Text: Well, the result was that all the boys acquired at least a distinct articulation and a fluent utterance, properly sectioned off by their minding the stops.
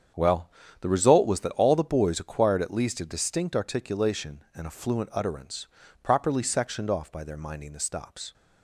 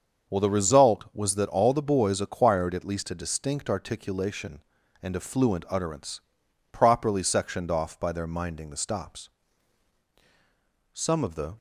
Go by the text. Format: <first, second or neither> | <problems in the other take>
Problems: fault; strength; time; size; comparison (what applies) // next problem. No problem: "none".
first | starts louder than the rest; until 1.3 s; 7 dB; strong in the first // goes on to say "Some of the"; noticeable; from 10.9 s on; 0.66 s long